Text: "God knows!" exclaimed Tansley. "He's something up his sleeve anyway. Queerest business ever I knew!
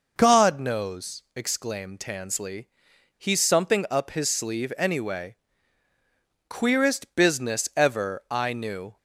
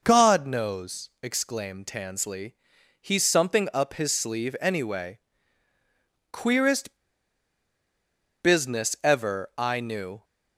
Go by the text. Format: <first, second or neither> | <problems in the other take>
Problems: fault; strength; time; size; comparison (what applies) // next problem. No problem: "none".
first | pauses between "Queerest" and "business"; strong; at 6.9 s; 1.4 s long